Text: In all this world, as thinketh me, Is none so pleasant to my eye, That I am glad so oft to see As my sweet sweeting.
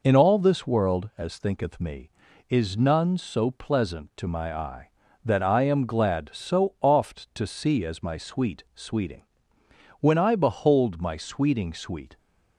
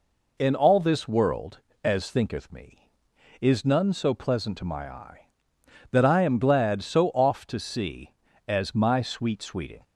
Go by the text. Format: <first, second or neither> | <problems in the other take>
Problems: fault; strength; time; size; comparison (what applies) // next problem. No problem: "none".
second | goes on to say "When I behold my sweeting sweet"; strong; from 9.9 s on; 2.1 s long